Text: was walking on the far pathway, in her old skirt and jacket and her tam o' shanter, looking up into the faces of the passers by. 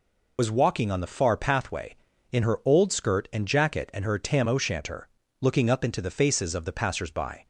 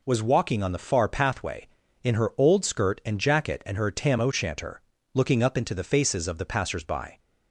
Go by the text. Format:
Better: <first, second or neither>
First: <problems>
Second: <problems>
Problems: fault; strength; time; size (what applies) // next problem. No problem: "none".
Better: second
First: loses the start of "was"; at 0.3 s; 65 ms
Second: none